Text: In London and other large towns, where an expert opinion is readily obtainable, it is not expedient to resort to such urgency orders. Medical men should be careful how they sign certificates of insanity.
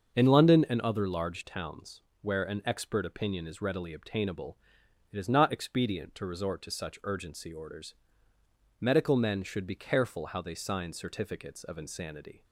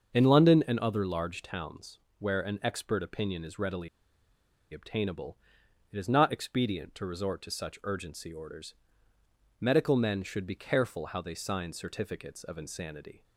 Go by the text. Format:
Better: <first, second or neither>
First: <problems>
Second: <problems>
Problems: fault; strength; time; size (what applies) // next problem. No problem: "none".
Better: first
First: starts louder than the rest; until 1.2 s; 6.5 dB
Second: starts louder than the rest; until 1.1 s; 6.5 dB // pauses between "readily" and "obtainable"; noticeable; at 3.8 s; 0.84 s long